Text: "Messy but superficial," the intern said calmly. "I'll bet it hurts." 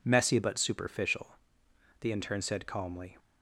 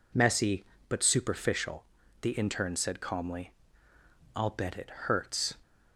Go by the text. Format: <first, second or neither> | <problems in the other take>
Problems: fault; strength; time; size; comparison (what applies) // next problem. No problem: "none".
second | stops before "I'll bet it hurts"; at 3.1 s